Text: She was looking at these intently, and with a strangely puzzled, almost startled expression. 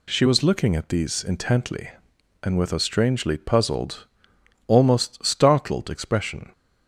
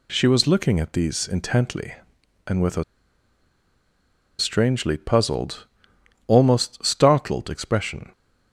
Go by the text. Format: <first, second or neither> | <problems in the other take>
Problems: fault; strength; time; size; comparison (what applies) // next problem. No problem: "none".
first | pauses between "a" and "strangely"; strong; at 2.8 s; 1.5 s long